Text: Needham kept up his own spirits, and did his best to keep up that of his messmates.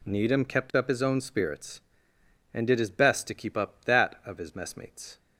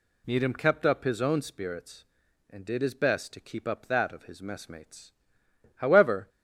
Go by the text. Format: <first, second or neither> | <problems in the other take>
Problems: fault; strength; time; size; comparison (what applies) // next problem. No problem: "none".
first | goes on to say "However"; from 5.7 s on; 0.52 s long